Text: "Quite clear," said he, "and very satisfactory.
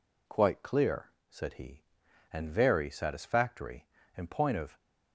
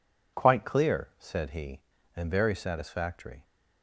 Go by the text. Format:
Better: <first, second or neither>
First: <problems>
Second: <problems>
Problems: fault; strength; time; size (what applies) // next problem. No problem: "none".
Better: second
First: goes on to say "In point of"; from 4.1 s on; 0.60 s long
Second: none